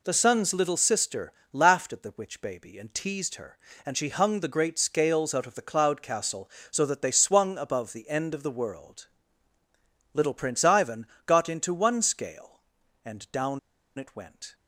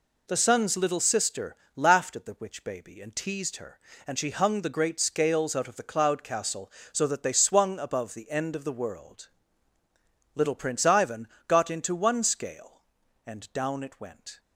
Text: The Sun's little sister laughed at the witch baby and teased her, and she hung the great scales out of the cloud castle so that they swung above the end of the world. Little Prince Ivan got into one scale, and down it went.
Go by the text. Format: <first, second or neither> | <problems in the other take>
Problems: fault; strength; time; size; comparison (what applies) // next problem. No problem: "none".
second | pauses between "sister" and "laughed"; slight; at 1.3 s; 0.22 s long; slight in the second // pauses between "Ivan" and "got"; slight; at 11.0 s; 0.20 s long; slight in the second // pauses between "down" and "it"; at 13.5 s; 0.39 s long